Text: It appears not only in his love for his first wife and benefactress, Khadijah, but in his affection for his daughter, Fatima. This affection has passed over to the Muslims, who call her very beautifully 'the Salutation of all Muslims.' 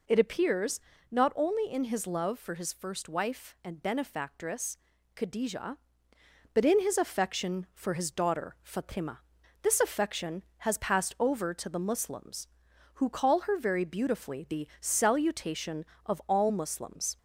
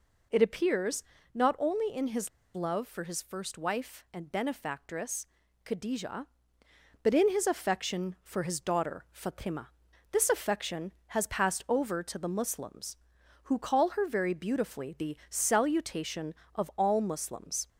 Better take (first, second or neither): first